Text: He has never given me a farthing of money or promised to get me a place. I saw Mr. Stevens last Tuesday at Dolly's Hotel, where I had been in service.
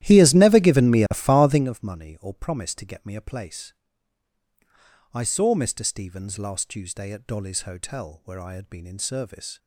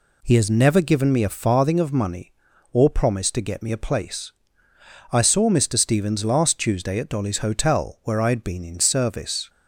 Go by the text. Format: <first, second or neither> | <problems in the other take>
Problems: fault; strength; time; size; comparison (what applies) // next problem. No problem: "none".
second | starts louder than the rest; strong; until 1.7 s; 13 dB